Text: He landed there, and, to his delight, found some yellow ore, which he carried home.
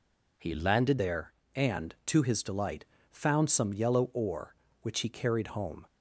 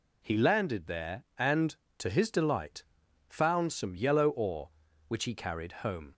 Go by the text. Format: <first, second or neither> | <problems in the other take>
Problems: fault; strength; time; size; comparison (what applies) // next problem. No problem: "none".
second | changes voice at "there"; from 0.9 s on; 4.9 s long